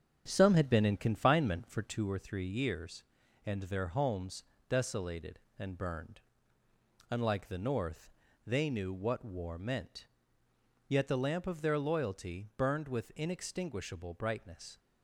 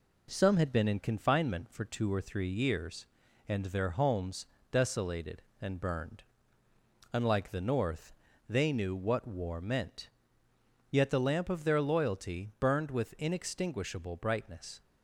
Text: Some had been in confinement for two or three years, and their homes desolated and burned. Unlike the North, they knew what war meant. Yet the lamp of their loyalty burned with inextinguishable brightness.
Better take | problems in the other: second | starts louder than the rest; strong; until 2.1 s; 8 dB // pauses between "homes" and "desolated"; slight; at 4.4 s; 0.26 s long; slight in the second

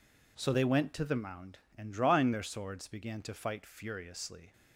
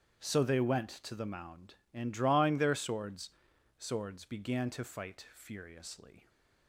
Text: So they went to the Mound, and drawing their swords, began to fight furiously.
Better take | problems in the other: first | starts louder than the rest; strong; until 1.3 s; 10 dB // says "swords" twice; at 3.8 s

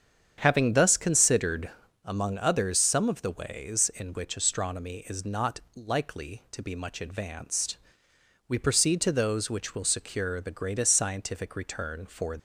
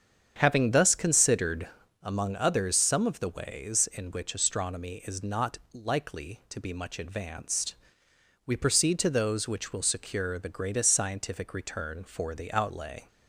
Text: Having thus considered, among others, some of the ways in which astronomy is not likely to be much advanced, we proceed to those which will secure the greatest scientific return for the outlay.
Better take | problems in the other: second | starts louder than the rest; strong; until 1.3 s; 8 dB; strong in the second // pauses between "not" and "likely"; slight; at 5.5 s; 0.16 s long; slight in the second // stops before "the outlay"; at 12.3 s

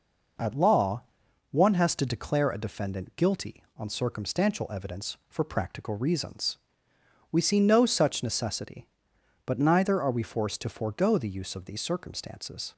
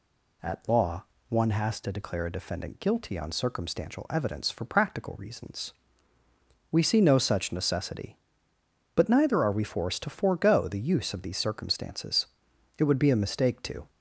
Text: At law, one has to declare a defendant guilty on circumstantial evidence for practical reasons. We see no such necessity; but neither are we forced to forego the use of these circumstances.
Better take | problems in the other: first | goes on to say "It would be a mistake to"; noticeable; from 12.7 s on; 1.1 s long

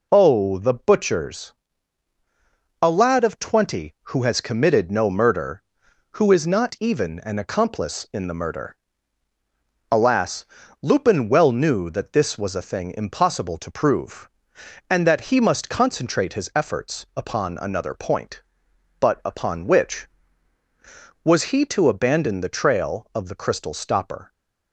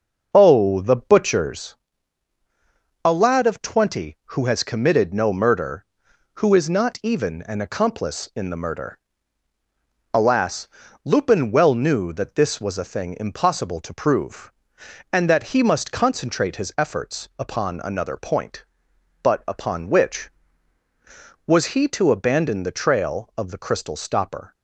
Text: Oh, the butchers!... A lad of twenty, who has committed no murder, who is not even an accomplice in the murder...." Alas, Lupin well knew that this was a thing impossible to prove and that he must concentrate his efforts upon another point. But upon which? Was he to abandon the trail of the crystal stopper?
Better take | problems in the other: first | starts louder than the rest; noticeable; until 1.8 s; 6 dB

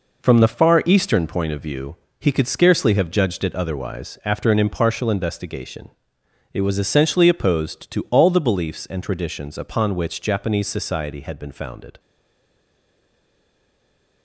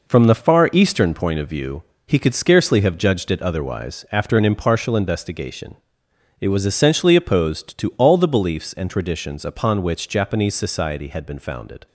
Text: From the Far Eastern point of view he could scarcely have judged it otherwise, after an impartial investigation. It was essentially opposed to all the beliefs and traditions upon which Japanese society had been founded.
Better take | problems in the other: second | pauses between "view" and "he"; slight; at 1.9 s; 0.22 s long; slight in the second // stays silent after the last word; from 11.9 s on; 2.3 s long

